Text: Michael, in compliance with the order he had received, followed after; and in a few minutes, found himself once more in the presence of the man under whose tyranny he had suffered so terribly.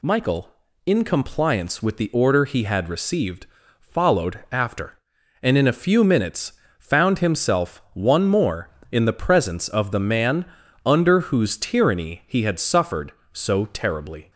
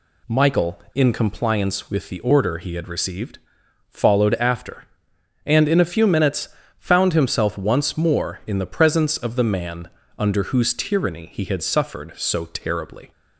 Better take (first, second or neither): second